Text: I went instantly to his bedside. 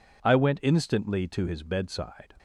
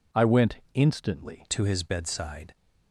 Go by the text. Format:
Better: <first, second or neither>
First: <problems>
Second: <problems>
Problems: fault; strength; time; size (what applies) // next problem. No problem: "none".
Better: first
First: none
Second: pauses between "went" and "instantly"; slight; at 0.5 s; 0.16 s long // changes voice at "to"; from 1.4 s on; 1.1 s long